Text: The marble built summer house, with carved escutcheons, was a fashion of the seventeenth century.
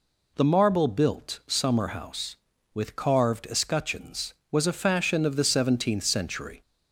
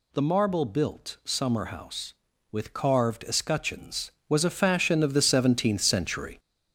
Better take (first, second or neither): first